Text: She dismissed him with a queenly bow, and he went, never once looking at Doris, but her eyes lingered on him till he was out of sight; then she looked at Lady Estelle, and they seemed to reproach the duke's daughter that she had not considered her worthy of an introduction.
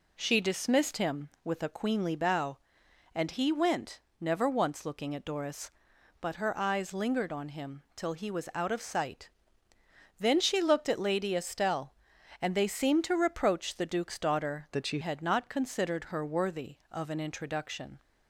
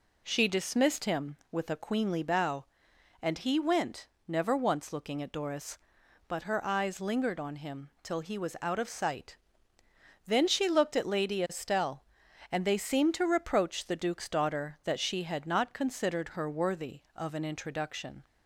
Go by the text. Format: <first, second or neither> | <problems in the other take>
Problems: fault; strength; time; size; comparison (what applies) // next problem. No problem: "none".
second | changes voice from "that" to "she"; from 14.7 to 14.9 s; 0.2 s long